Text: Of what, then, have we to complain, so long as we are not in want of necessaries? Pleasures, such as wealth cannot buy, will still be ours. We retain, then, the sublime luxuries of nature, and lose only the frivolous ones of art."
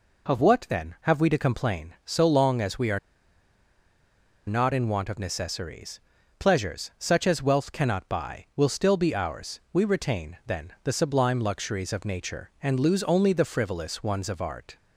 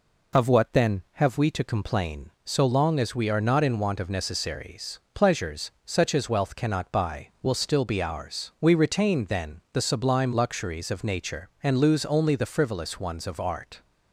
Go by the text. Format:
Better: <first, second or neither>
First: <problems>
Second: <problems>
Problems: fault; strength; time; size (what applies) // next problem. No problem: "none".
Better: second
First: pauses between "are" and "not"; strong; at 2.9 s; 1.4 s long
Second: none